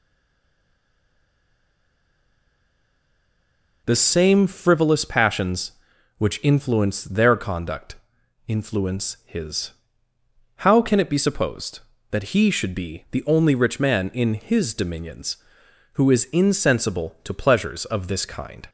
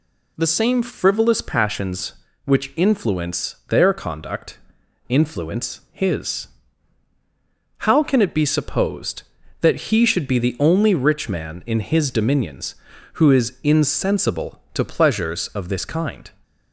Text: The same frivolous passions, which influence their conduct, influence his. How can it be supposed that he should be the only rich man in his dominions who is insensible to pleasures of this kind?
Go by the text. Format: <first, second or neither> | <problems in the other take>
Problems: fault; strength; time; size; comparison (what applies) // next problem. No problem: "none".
second | stays silent before the first word; strong; until 3.8 s; 3.8 s long